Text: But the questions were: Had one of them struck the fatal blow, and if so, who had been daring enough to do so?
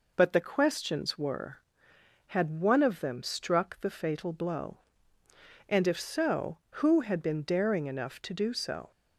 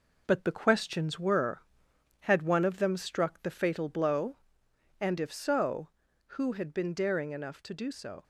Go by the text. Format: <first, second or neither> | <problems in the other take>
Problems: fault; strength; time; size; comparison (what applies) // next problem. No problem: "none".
first | gets quieter; noticeable; throughout; 5 dB